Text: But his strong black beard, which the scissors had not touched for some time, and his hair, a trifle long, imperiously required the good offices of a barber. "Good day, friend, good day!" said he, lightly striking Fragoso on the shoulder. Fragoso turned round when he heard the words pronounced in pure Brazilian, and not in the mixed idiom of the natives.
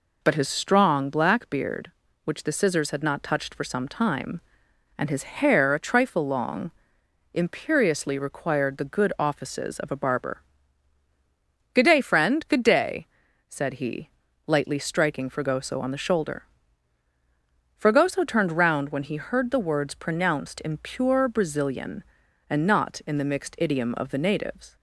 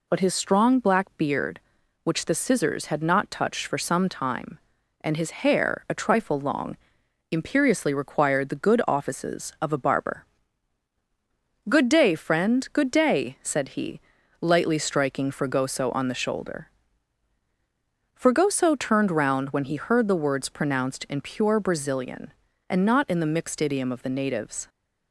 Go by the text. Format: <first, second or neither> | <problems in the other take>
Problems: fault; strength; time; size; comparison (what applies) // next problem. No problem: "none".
neither | none